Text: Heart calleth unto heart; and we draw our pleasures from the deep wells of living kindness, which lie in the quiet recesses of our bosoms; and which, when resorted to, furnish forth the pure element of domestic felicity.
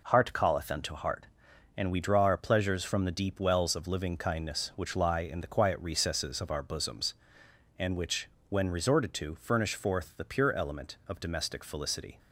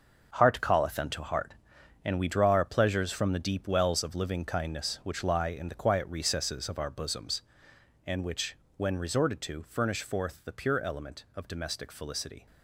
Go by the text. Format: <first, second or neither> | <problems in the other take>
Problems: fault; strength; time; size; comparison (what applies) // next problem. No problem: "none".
first | gets quieter; strong; throughout; 10 dB